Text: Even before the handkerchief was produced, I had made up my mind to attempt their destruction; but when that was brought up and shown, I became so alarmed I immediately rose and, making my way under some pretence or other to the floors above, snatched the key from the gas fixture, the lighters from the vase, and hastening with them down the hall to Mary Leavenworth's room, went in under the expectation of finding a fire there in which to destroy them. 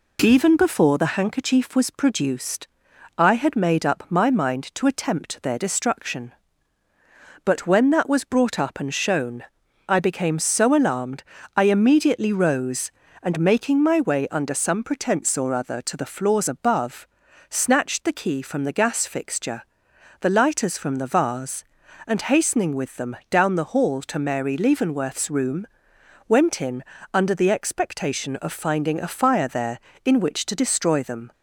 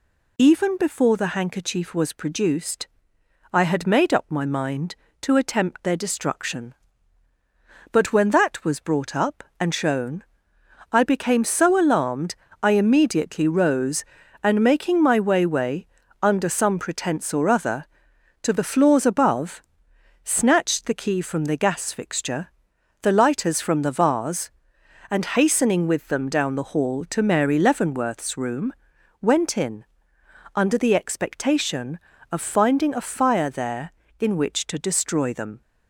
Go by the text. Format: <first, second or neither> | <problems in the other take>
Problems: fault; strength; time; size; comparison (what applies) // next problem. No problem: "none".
first | pauses between "alarmed" and "I"; slight; at 12.3 s; 0.28 s long; slight in the first // says "way" twice; at 15.4 s // pauses between "in" and "under"; noticeable; at 29.8 s; 0.70 s long; slight in the first